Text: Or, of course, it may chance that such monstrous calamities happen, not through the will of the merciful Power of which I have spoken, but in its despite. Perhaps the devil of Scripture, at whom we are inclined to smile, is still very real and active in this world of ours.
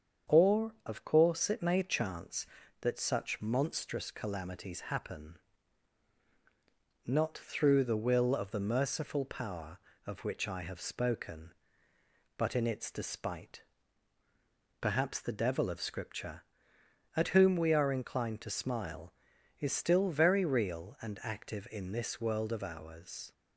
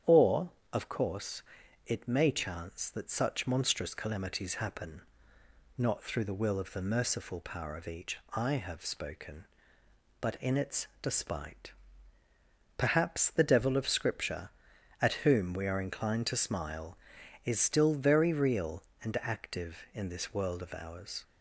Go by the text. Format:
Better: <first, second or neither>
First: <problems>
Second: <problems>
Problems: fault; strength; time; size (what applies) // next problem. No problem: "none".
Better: first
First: starts louder than the rest; strong; until 1.3 s; 7.5 dB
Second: starts louder than the rest; strong; until 1.2 s; 9 dB // says "each" for "which"; at 7.8 s